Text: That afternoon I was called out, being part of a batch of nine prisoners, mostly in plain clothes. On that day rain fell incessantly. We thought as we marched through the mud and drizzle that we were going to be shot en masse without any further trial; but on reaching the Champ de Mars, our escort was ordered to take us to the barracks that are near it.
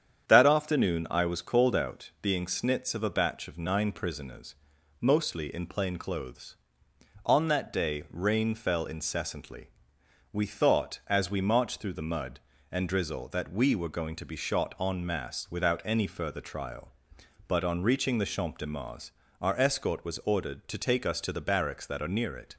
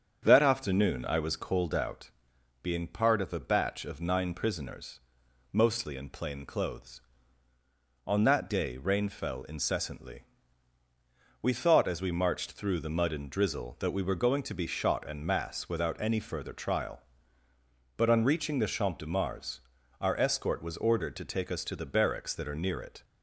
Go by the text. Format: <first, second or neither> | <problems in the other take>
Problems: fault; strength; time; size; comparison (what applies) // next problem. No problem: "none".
second | starts louder than the rest; strong; until 1.3 s; 8.5 dB; strong in the second // says "snits" for "part"; at 2.4 s